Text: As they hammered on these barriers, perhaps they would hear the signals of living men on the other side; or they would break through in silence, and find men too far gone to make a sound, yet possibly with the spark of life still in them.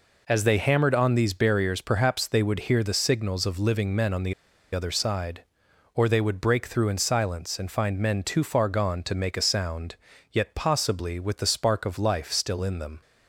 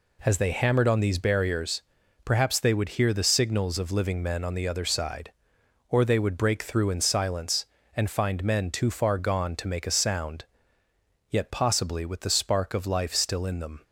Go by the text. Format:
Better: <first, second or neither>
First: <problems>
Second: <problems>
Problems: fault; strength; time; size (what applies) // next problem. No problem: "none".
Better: second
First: pauses between "the" and "other"; at 4.3 s; 0.41 s long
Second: none